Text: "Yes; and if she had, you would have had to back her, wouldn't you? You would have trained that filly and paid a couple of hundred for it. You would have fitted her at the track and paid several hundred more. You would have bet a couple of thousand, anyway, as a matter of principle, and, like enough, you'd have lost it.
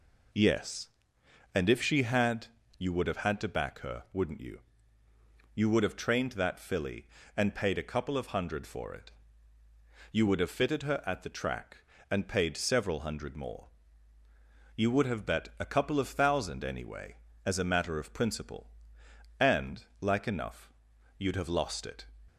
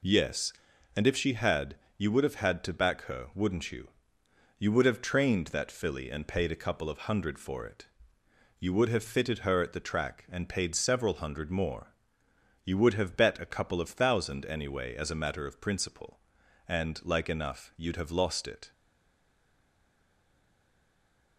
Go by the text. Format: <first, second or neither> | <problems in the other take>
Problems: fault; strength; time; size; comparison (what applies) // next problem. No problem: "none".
first | stays silent after the last word; strong; from 18.7 s on; 2.6 s long